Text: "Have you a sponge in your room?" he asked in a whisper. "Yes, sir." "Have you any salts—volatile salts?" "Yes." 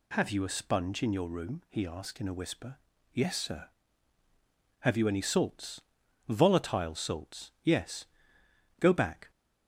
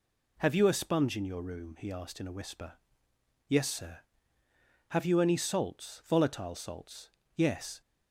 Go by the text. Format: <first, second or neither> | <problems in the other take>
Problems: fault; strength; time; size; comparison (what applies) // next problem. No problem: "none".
second | goes on to say "Go back"; from 8.7 s on; 0.52 s long